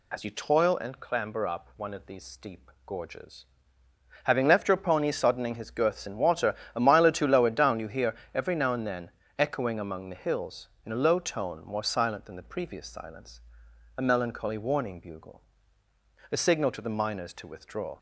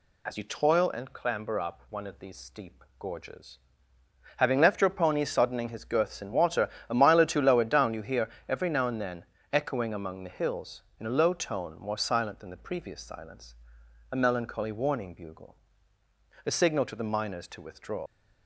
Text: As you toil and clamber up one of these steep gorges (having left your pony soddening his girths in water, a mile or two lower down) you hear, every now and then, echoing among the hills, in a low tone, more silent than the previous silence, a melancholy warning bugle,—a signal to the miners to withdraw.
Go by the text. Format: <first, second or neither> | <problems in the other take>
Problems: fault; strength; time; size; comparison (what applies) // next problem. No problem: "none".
first | leaves "withdraw" unfinished; at 18.0 s; 60 ms